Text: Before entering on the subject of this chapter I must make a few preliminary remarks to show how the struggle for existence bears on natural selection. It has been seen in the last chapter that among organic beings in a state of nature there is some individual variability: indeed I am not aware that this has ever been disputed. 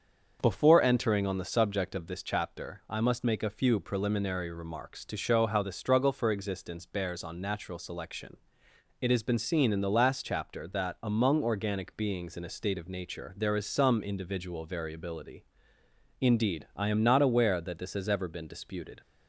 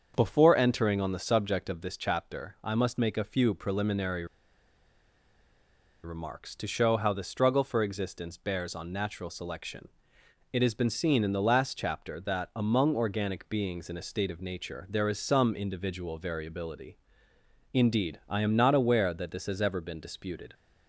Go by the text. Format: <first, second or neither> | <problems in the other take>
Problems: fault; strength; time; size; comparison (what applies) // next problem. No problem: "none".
first | starts louder than the rest; until 1.1 s; 6.5 dB; also in the first // pauses between "preliminary" and "remarks"; strong; at 4.2 s; 1.7 s long